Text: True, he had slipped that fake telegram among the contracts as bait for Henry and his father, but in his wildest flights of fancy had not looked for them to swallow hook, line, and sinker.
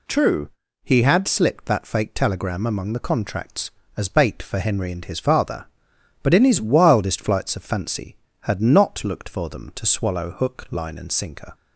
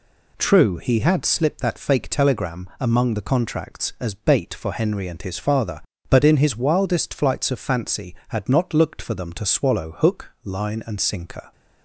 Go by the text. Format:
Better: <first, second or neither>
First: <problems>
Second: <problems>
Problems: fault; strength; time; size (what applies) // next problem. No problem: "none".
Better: neither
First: none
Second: none